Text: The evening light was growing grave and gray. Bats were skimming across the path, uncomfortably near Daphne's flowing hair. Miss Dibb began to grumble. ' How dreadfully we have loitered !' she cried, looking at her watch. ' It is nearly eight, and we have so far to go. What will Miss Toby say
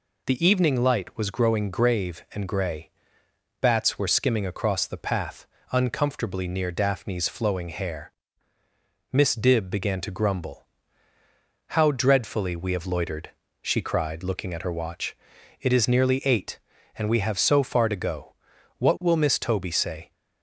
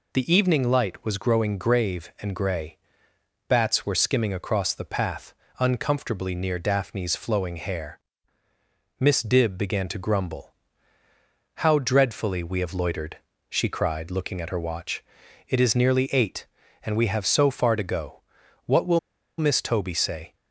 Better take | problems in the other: first | pauses between "will" and "Miss"; at 18.9 s; 0.38 s long

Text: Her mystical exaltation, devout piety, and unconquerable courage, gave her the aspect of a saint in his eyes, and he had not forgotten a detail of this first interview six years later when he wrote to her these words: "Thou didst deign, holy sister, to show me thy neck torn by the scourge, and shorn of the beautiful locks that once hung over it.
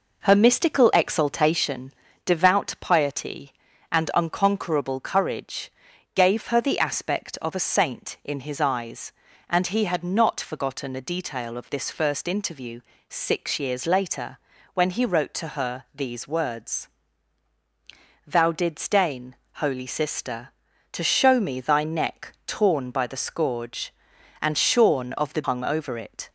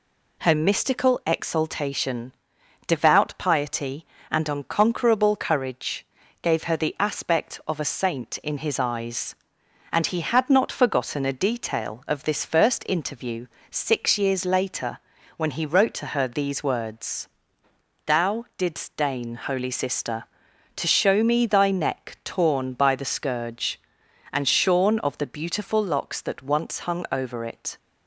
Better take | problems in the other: second | pauses between "interview" and "six"; slight; at 12.8 s; 0.28 s long; slight in the second // pauses between "later" and "when"; slight; at 14.3 s; 0.36 s long; also in the second // skips "beautiful locks that once"; at 25.4 s

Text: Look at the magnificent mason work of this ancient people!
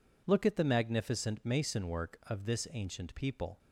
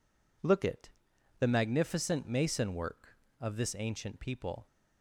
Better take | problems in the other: first | says "it" for "at"; at 0.6 s

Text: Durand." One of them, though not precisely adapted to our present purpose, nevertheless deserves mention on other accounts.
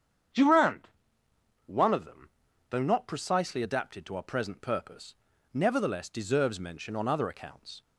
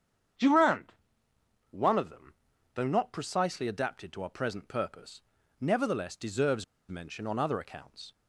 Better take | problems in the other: first | starts louder than the rest; strong; until 2.1 s; 8 dB; strong in the first // pauses between "deserves" and "mention"; slight; at 6.6 s; 0.25 s long

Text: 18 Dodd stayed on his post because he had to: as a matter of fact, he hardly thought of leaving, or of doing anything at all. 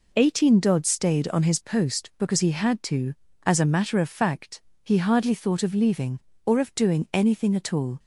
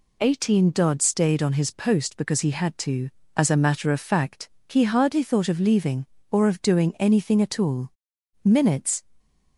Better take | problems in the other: first | goes on to say "Minutes"; from 8.4 s on; 0.58 s long

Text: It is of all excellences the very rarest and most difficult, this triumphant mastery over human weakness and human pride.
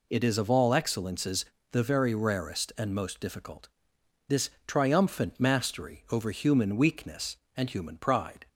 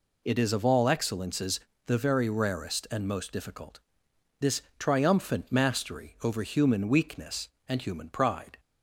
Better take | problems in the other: neither | pauses between "excellences" and "the"; slight; the same in both // pauses between "this" and "triumphant"; slight; the same in both

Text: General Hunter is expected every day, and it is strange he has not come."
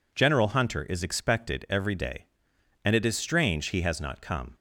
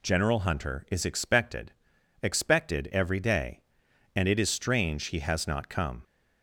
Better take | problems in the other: first | says "expected" twice; at 2.2 s

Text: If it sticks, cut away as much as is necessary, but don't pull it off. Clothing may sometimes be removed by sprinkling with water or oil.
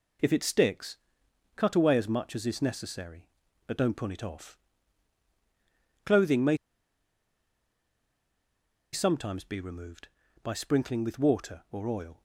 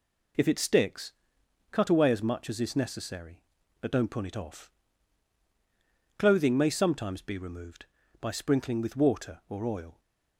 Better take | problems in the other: second | pauses between "may" and "sometimes"; strong; at 6.5 s; 2.3 s long

